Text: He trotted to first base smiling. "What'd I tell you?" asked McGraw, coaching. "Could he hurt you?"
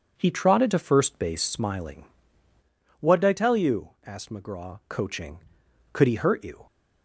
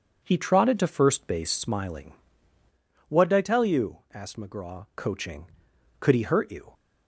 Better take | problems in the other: neither | none

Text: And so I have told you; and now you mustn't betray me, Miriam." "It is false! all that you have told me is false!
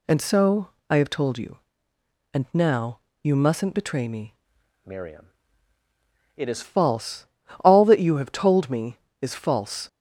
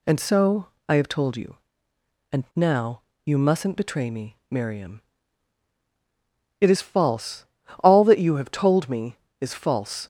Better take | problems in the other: second | pauses between "so" and "I"; slight; at 0.6 s; 0.22 s long; slight in the second // pauses between "now" and "you"; slight; at 2.9 s; 0.24 s long; slight in the second // changes voice from "Miriam" to "is"; from 4.8 to 6.6 s; 1.8 s long

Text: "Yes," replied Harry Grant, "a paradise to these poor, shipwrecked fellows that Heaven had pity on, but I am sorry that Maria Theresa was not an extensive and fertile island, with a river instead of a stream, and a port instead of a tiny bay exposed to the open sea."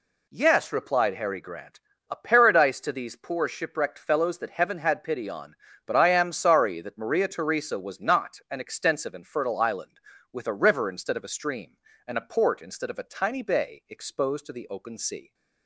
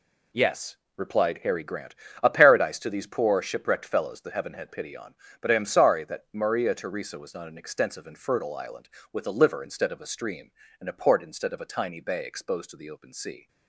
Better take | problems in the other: first | says "liver" for "river"; at 9.3 s

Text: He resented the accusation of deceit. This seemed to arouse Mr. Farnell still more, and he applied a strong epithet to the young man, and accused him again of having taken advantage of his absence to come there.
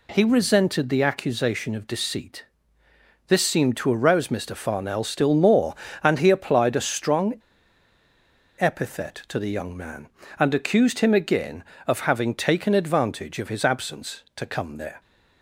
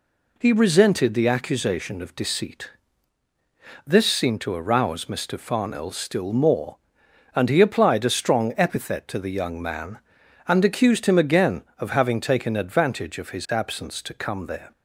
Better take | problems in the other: second | pauses between "strong" and "epithet"; strong; at 7.3 s; 1.2 s long

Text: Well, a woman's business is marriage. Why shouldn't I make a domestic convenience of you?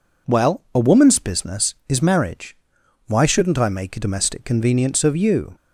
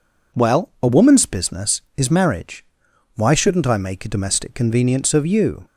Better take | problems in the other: neither | none

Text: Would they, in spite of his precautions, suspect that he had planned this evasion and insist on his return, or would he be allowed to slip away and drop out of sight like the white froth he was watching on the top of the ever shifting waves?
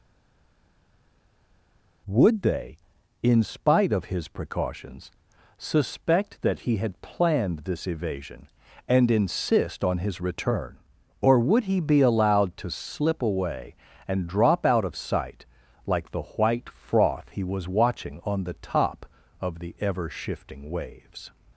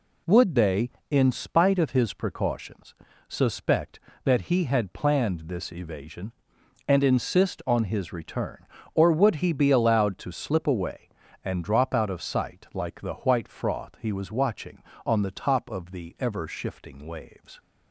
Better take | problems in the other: second | stays silent before the first word; noticeable; until 2.0 s; 2.0 s long // pauses between "sight" and "like"; at 15.4 s; 0.42 s long

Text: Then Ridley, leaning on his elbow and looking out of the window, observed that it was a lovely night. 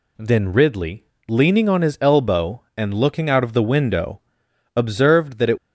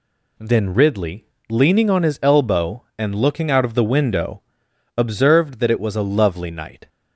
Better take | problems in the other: second | stops before "was a lovely night"; at 5.5 s

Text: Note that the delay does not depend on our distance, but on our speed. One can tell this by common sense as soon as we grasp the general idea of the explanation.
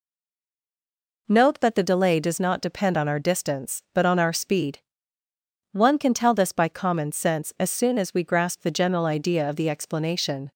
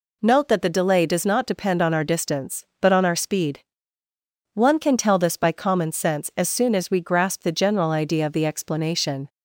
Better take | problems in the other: second | stays silent before the first word; noticeable; until 1.2 s; 1.2 s long

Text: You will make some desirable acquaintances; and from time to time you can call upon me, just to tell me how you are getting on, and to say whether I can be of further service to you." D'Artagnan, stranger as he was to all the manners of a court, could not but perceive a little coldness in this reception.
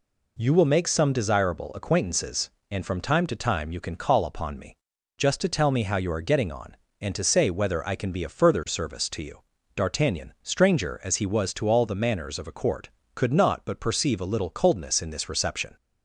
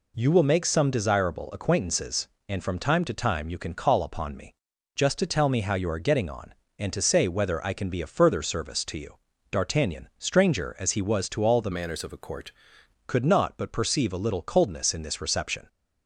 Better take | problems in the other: first | changes voice from "manners" to "court"; from 11.7 to 12.5 s; 0.8 s long

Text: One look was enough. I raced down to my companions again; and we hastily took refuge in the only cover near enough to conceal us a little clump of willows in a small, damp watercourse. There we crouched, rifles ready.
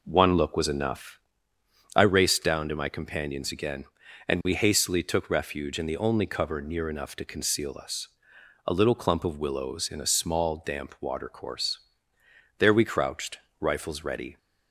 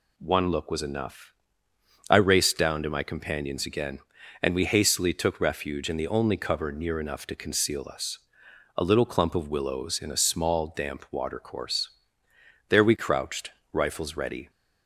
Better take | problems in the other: second | starts louder than the rest; noticeable; until 1.3 s; 4.5 dB // pauses between "us" and "a"; noticeable; at 8.0 s; 0.60 s long; noticeable in the second

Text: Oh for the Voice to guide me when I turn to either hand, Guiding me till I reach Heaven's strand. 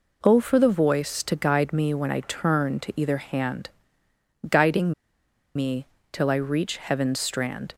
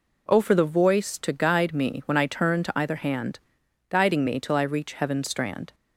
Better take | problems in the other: second | pauses between "Guiding" and "me"; noticeable; at 4.9 s; 0.62 s long // pauses between "me" and "till"; slight; at 5.8 s; 0.24 s long

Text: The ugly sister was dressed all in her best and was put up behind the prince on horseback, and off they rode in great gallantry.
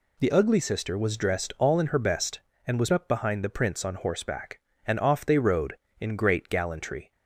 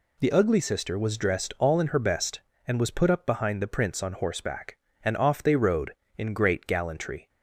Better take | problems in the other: second | skips "put"; at 2.9 s

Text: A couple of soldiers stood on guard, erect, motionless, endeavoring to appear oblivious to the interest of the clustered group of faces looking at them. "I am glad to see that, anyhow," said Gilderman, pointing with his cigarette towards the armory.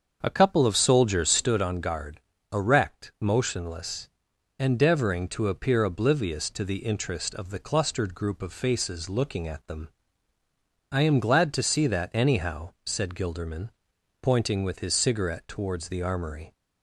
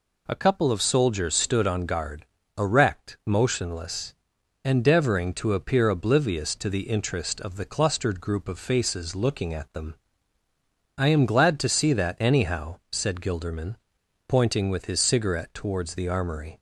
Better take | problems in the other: second | starts louder than the rest; until 1.5 s; 7 dB

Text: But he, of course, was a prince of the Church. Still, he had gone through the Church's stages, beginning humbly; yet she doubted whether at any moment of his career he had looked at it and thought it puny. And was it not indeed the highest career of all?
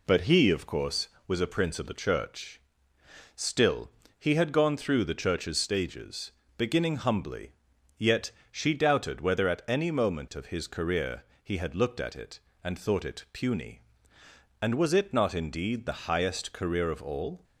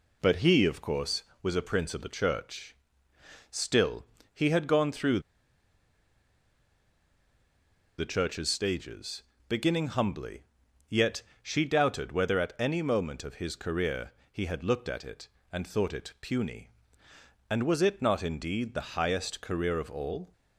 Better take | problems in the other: first | pauses between "through" and "the"; strong; at 5.1 s; 2.7 s long // pauses between "yet" and "she"; slight; at 11.2 s; 0.22 s long; slight in the first // pauses between "career" and "he"; slight; at 14.1 s; 0.20 s long; slight in the first

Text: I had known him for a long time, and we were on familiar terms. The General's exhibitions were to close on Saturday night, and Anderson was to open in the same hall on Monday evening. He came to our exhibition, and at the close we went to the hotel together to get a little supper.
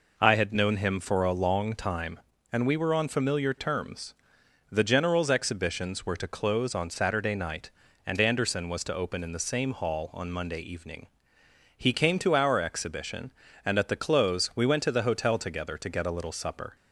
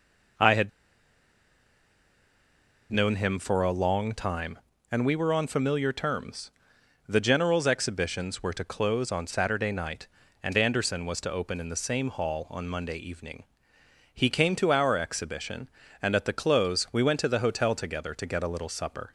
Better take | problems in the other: first | pauses between "had" and "known"; strong; at 0.6 s; 2.2 s long

